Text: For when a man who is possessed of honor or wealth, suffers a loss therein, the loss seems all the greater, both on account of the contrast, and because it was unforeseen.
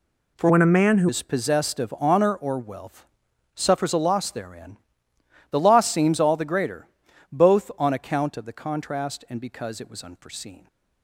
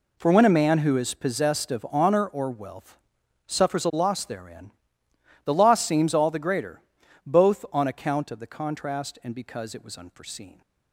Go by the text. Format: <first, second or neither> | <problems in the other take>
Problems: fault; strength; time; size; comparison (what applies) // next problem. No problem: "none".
second | changes voice from "when" to "who"; from 0.4 to 1.0 s; 0.6 s long